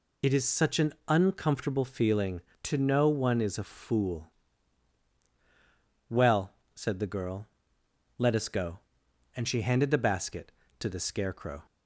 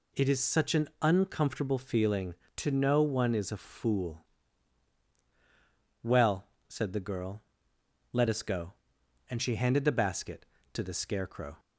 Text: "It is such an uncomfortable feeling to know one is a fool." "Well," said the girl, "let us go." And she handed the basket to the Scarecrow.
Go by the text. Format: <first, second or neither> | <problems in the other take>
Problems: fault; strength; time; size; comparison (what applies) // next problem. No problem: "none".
second | loses the start of "It"; at 0.2 s; 40 ms